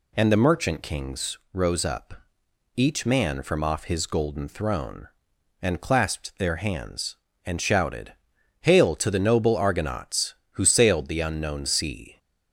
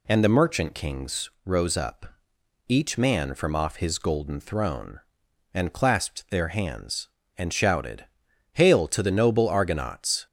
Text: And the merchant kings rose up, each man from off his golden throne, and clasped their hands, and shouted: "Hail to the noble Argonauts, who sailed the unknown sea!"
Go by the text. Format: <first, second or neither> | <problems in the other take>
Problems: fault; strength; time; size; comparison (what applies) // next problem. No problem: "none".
first | stops before "who sailed the unknown sea"; at 10.2 s